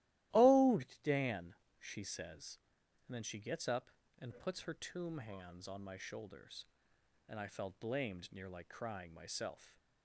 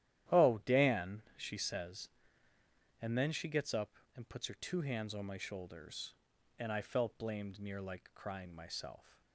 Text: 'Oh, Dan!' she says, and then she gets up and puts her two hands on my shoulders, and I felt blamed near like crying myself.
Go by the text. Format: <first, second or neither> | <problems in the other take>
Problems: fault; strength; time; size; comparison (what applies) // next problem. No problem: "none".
second | starts louder than the rest; strong; until 1.5 s; 15.5 dB; strong in the second // says "tomb" for "two"; at 4.7 s